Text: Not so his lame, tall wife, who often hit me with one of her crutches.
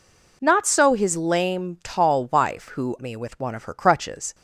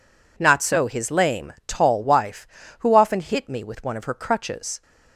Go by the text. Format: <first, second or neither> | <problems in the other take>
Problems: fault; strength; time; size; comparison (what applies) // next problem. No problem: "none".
second | skips "often hit"; at 2.9 s